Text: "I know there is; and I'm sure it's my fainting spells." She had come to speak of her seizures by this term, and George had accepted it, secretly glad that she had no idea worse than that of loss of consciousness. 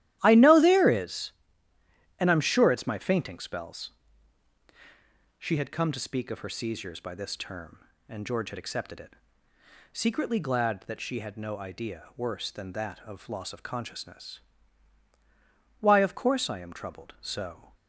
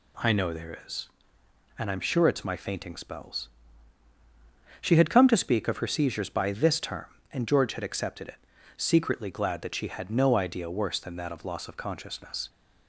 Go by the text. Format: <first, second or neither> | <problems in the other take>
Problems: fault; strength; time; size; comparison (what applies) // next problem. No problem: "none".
second | starts louder than the rest; strong; until 1.2 s; 13 dB // goes on to say "Why of course I am troubled so"; strong; from 15.8 s on; 1.9 s long